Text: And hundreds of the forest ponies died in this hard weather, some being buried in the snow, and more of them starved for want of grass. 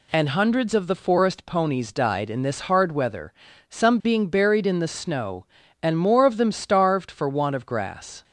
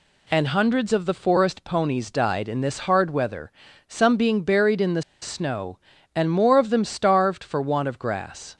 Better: first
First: none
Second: pauses between "the" and "snow"; slight; at 5.0 s; 0.19 s long

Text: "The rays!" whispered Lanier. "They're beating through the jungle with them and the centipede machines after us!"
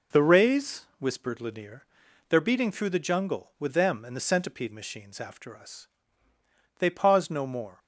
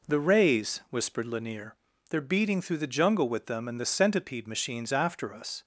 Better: second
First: goes on to say "They paused no more"; noticeable; from 6.7 s on; 1.0 s long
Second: none

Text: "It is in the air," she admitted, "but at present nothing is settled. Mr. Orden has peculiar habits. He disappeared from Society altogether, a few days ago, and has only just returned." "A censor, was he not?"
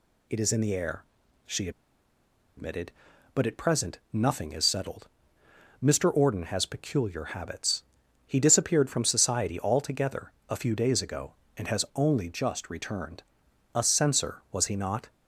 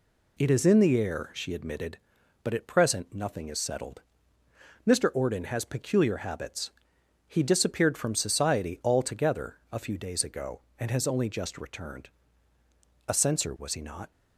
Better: second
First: pauses between "she" and "admitted"; noticeable; at 1.6 s; 0.87 s long // pauses between "present" and "nothing"; slight; at 3.9 s; 0.16 s long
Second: none

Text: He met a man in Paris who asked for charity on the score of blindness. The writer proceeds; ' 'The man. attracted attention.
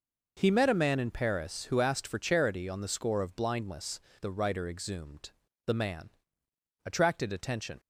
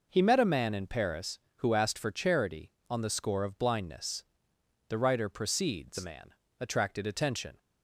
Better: second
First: says "exhumed" for "proceeds"; at 4.6 s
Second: none

